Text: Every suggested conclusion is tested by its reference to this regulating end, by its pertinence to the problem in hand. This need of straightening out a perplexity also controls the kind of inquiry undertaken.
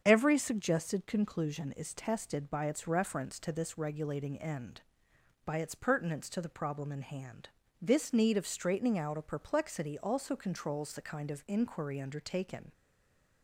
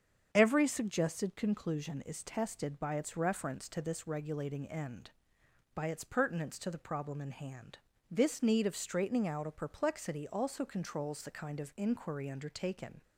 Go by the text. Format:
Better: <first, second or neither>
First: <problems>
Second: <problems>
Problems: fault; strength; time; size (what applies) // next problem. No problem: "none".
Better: second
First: starts louder than the rest; strong; until 1.0 s; 7.5 dB // stays silent after the last word; slight; from 12.7 s on; 0.7 s long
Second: starts louder than the rest; strong; until 1.3 s; 7.5 dB